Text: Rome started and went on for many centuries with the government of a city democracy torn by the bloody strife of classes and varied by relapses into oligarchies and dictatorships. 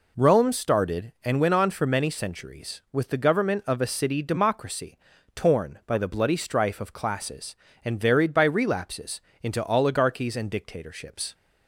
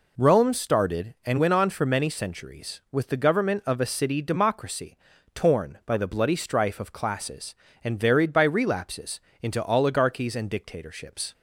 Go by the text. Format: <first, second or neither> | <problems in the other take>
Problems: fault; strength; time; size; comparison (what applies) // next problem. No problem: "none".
neither | pauses between "democracy" and "torn"; the same in both // pauses between "relapses" and "into"; slight; the same in both